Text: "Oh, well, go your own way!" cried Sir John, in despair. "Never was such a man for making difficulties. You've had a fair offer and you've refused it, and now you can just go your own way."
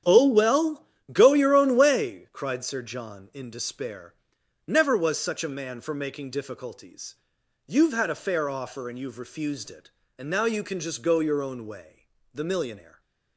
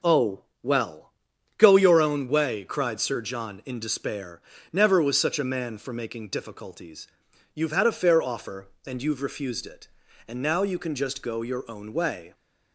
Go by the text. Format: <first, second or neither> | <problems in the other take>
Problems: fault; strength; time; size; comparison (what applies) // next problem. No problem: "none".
second | starts louder than the rest; strong; until 1.3 s; 9.5 dB // goes on to say "The millionaire"; noticeable; from 12.3 s on; 0.66 s long